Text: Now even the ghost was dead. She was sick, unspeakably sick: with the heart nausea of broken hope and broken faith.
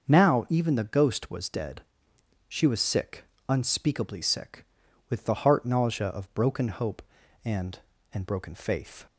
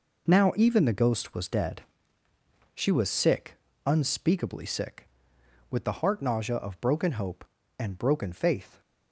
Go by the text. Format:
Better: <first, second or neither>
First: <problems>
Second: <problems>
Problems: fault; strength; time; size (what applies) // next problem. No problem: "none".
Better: second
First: starts louder than the rest; until 1.1 s; 6 dB // says "and" twice; at 8.1 s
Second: none